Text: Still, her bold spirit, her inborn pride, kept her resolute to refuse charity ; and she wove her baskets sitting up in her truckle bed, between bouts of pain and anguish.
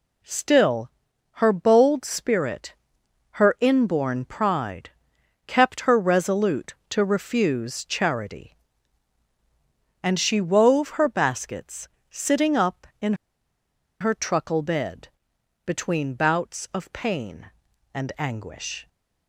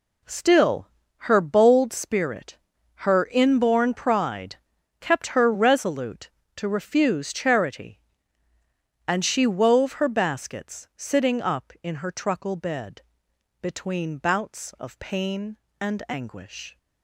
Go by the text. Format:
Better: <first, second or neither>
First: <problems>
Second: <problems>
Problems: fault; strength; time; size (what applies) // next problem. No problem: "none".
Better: second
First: pauses between "baskets" and "sitting"; slight; at 11.8 s; 0.20 s long // pauses between "in" and "her"; noticeable; at 13.1 s; 0.86 s long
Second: none